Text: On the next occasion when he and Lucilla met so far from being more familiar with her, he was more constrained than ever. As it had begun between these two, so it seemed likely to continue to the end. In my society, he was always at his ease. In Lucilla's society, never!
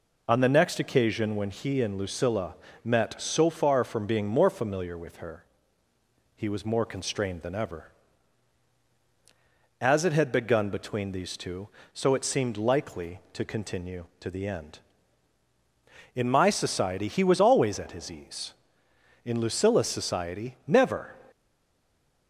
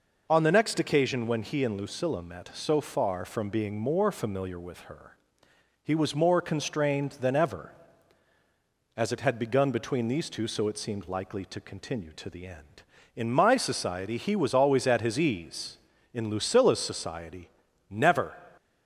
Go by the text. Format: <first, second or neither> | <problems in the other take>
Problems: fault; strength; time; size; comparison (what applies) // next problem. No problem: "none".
second | pauses between "Lucilla" and "met"; slight; at 2.5 s; 0.28 s long // stays silent after the last word; from 21.3 s on; 0.9 s long